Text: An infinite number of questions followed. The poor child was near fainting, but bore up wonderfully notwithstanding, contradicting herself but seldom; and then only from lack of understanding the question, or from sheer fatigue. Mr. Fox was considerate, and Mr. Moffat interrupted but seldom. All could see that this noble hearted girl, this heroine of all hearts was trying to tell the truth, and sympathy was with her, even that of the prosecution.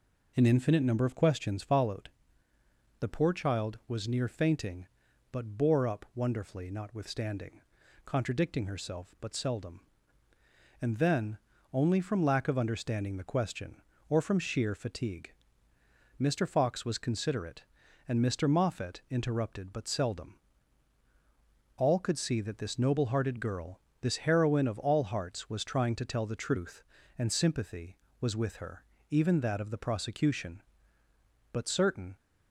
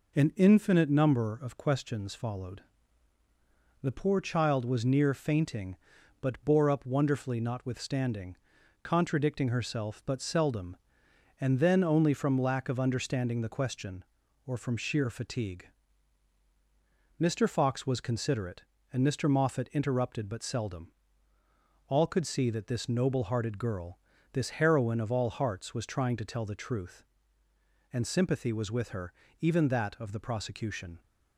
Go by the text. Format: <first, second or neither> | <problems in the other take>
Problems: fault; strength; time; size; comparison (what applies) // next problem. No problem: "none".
second | pauses between "then" and "only"; slight; at 11.3 s; 0.34 s long // goes on to say "But certain"; noticeable; from 31.5 s on; 0.64 s long